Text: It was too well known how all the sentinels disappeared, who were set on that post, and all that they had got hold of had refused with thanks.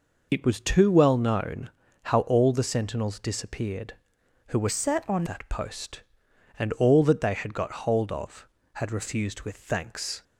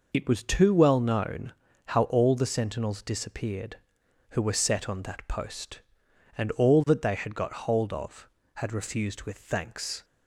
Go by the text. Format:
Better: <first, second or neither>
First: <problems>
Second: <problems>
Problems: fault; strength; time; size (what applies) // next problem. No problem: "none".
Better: second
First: pauses between "known" and "how"; slight; at 1.7 s; 0.32 s long // changes voice from "set" to "on"; from 4.6 to 5.2 s; 0.6 s long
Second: pauses between "known" and "how"; slight; at 1.5 s; 0.32 s long